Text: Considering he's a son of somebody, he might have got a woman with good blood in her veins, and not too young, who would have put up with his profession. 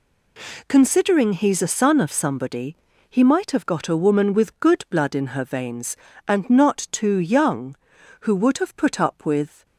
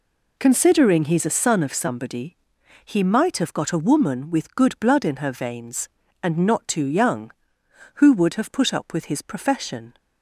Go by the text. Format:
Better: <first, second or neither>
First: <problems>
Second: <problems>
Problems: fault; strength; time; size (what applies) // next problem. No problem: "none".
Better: second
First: stops before "his profession"; at 9.6 s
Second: none